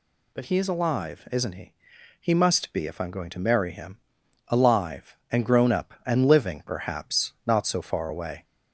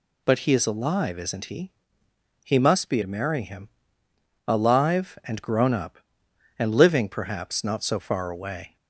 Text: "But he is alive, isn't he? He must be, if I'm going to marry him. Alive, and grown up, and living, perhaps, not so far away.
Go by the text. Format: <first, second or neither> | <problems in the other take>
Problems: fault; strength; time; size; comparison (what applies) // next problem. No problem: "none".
first | skips "if I'm going"; at 3.0 s